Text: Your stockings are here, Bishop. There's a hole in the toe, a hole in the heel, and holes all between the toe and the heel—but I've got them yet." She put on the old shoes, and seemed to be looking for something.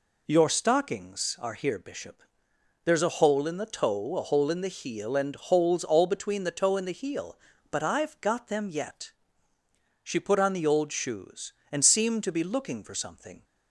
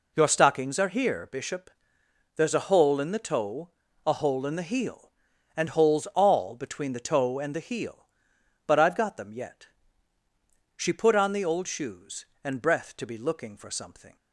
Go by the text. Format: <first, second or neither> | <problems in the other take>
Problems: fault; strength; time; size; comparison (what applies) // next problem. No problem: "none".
first | says "breath" for "seemed"; at 12.6 s